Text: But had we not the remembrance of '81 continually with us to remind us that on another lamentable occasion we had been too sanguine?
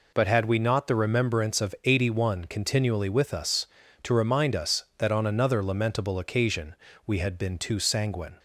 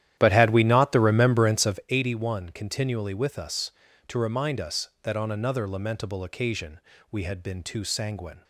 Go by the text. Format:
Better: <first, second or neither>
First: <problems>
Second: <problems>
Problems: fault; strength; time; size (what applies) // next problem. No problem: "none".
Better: first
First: pauses between "occasion" and "we"; slight; at 6.7 s; 0.32 s long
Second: starts louder than the rest; strong; until 1.9 s; 11.5 dB // pauses between "occasion" and "we"; slight; at 6.7 s; 0.32 s long